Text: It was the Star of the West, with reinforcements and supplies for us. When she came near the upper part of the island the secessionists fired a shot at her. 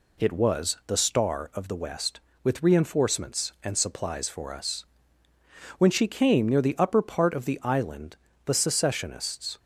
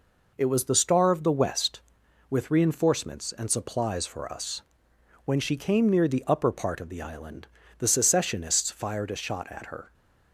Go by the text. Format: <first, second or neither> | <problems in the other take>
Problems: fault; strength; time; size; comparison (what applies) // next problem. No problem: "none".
second | pauses between "island" and "the"; slight; at 8.1 s; 0.28 s long; slight in the second // stops before "fired a shot at her"; at 9.5 s